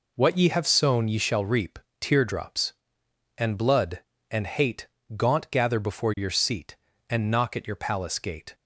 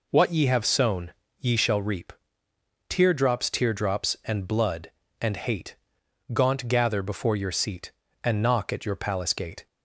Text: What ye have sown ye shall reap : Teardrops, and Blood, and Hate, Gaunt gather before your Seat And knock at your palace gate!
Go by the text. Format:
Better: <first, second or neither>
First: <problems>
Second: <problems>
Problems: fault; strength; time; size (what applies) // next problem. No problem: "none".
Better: first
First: none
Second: pauses between "sown" and "ye"; slight; at 1.1 s; 0.25 s long // says "Teardrops" twice; at 3.4 s